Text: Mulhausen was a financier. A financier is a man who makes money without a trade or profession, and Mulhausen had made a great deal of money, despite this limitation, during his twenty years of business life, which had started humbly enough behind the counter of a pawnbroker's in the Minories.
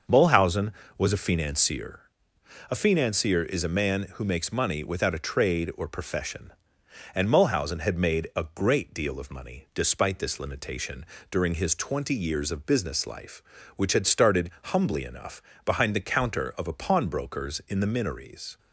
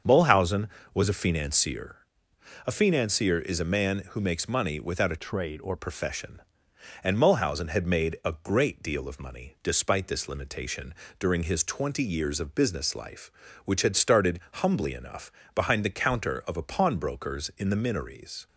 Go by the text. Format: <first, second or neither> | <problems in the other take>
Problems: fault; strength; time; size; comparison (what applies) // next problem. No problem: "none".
first | starts louder than the rest; until 1.3 s; 6.5 dB // changes voice from "trade" to "or"; from 5.1 to 5.7 s; 0.6 s long // pauses between "enough" and "behind"; slight; at 15.2 s; 0.26 s long; slight in the first